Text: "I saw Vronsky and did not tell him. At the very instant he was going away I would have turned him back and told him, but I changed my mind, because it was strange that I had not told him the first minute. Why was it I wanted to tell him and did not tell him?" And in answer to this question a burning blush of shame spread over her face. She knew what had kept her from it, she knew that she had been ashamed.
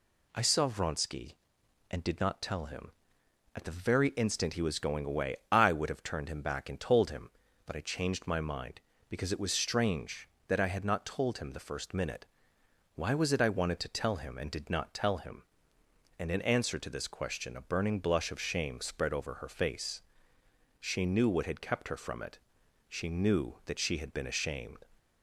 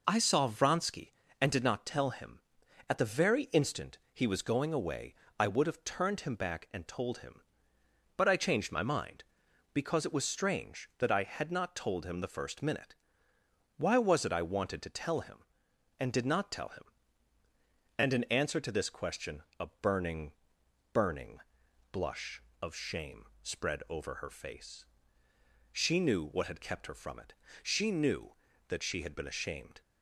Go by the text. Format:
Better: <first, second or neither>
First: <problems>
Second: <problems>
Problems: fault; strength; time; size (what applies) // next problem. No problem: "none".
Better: first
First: none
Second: pauses between "instant" and "he"; slight; at 3.9 s; 0.16 s long // pauses between "away" and "I"; slight; at 5.1 s; 0.24 s long // pauses between "question" and "a"; slight; at 19.4 s; 0.16 s long // says "burning" twice; at 20.9 s // pauses between "shame" and "spread"; slight; at 23.2 s; 0.18 s long